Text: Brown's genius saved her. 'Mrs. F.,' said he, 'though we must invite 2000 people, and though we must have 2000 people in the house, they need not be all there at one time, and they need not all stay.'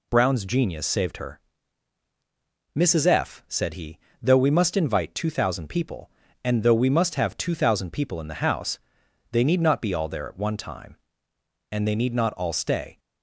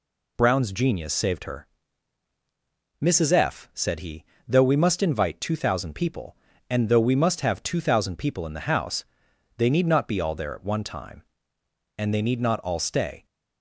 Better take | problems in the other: neither | none

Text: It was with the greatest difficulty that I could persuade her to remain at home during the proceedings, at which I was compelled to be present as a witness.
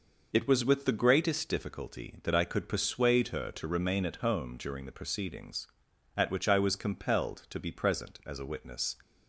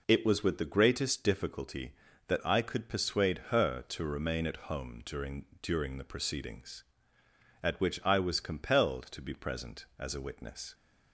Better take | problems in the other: first | says "during" twice; at 5.6 s

